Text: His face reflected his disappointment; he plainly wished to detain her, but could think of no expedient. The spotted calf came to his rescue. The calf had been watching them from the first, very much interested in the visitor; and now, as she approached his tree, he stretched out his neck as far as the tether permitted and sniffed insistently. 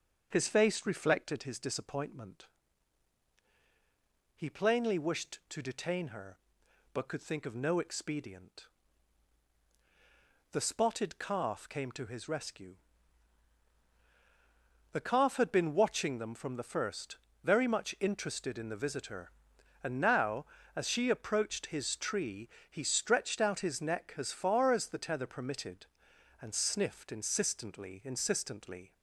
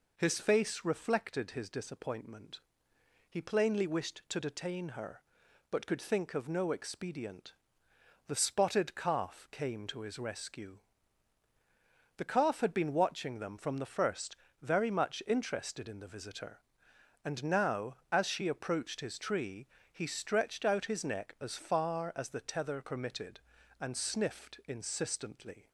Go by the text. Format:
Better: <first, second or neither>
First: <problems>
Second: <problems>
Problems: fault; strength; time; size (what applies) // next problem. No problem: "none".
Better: second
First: starts louder than the rest; until 1.3 s; 7 dB // says "insistently" twice; at 28.0 s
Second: none